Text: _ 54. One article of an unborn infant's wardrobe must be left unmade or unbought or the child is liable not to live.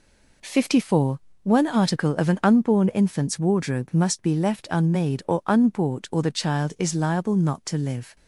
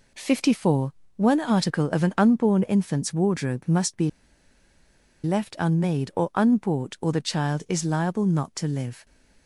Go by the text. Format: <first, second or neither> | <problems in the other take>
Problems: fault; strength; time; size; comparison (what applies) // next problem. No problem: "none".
first | pauses between "be" and "left"; at 4.0 s; 1.1 s long